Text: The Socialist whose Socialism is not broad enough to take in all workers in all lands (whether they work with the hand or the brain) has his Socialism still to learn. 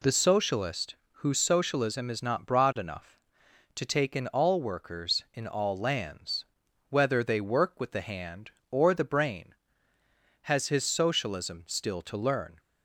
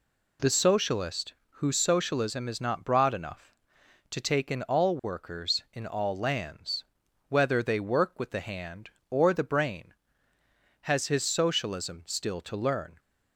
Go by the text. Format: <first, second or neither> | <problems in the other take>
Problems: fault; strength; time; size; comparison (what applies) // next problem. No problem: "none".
neither | pauses between "Socialist" and "whose"; slight; the same in both